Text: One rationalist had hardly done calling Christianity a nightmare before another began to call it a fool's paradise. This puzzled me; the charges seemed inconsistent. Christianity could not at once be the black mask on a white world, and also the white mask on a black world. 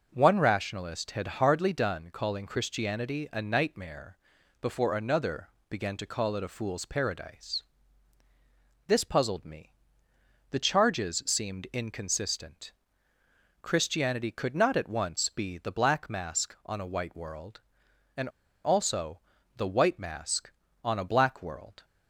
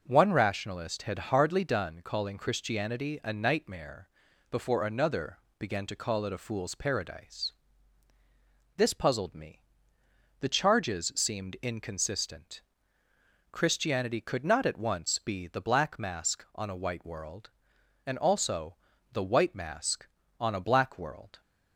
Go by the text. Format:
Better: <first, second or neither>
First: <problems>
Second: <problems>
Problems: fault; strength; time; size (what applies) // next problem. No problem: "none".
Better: second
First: pauses between "nightmare" and "before"; at 4.1 s; 0.42 s long // pauses between "another" and "began"; slight; at 5.4 s; 0.20 s long // pauses between "and" and "also"; slight; at 18.2 s; 0.35 s long // pauses between "also" and "the"; slight; at 19.2 s; 0.36 s long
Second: pauses between "nightmare" and "before"; at 4.0 s; 0.40 s long // pauses between "another" and "began"; slight; at 5.3 s; 0.20 s long // pauses between "also" and "the"; slight; at 18.7 s; 0.36 s long